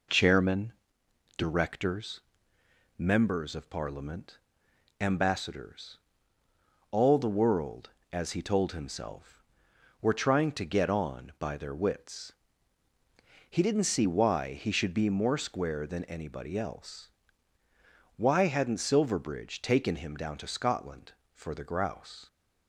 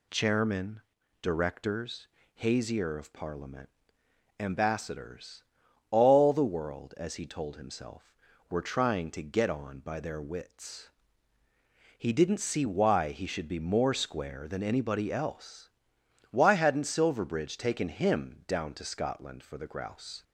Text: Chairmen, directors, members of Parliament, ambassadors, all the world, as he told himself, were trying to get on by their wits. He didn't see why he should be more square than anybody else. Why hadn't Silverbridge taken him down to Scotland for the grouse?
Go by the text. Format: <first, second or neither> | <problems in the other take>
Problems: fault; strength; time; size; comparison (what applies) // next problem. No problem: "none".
first | says "hazier" for "members"; at 2.3 s